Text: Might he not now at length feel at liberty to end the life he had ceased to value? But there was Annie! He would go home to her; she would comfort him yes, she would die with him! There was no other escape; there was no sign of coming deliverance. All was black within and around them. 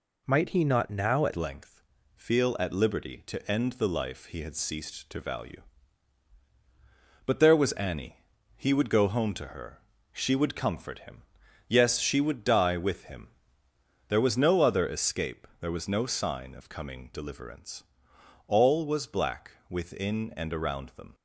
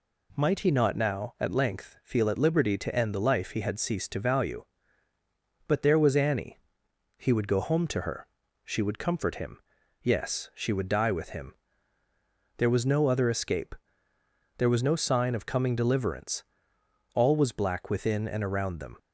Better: second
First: changes voice at "length"; from 1.3 s on; 19.8 s long // pauses between "length" and "feel"; slight; at 1.8 s; 0.34 s long // pauses between "him" and "yes"; noticeable; at 11.2 s; 0.46 s long // pauses between "black" and "within"; slight; at 19.5 s; 0.18 s long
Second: pauses between "him" and "yes"; at 9.5 s; 0.42 s long

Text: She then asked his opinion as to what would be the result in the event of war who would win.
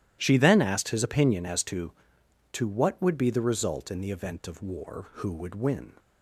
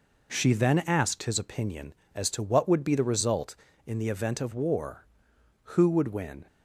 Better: second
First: starts louder than the rest; strong; until 1.2 s; 13 dB // says "to" twice; at 2.5 s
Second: none

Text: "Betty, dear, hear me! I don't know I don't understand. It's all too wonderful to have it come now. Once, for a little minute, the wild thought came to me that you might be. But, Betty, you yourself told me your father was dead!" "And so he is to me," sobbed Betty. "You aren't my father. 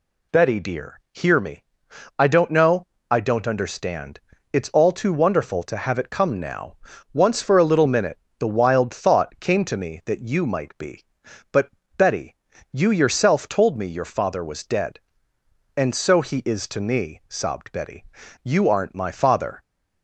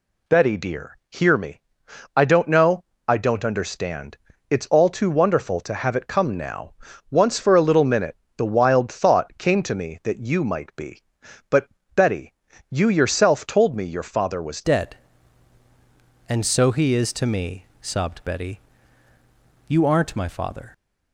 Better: first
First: pauses between "know" and "I"; slight; at 2.8 s; 0.24 s long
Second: pauses between "know" and "I"; slight; at 2.8 s; 0.24 s long // changes voice at "dead"; from 14.6 s on; 6.1 s long

